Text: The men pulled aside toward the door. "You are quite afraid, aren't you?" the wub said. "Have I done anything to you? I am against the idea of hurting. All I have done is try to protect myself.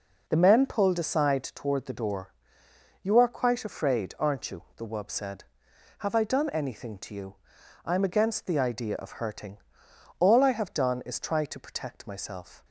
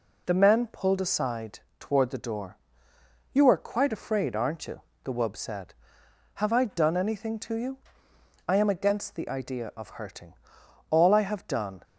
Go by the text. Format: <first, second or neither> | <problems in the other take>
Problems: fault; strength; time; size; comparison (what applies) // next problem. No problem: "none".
first | pauses between "aside" and "toward"; slight; at 1.5 s; 0.20 s long // stops before "is try to protect myself"; at 11.8 s